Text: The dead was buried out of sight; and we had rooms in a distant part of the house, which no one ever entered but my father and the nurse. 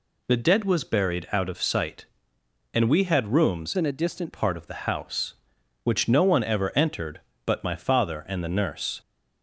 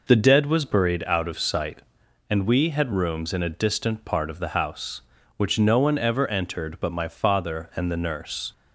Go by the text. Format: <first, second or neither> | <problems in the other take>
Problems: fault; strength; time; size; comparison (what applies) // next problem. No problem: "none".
second | changes voice from "in" to "distant"; from 3.7 to 4.3 s; 0.6 s long